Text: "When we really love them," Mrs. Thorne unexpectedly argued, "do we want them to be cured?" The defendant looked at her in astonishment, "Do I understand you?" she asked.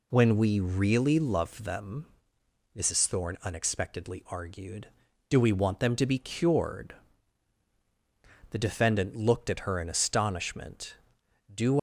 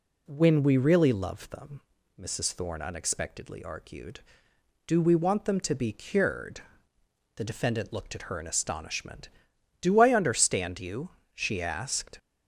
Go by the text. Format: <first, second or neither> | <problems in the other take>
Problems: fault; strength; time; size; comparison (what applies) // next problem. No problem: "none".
second | stops before "I understand you she asked"; at 11.7 s